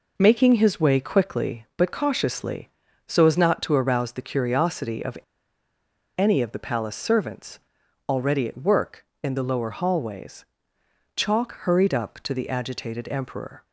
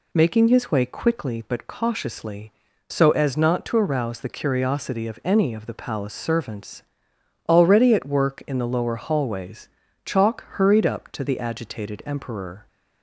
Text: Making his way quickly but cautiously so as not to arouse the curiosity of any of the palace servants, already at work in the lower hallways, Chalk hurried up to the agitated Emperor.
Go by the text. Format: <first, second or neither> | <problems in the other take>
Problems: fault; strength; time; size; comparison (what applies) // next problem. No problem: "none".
second | pauses between "of" and "any"; at 5.1 s; 0.99 s long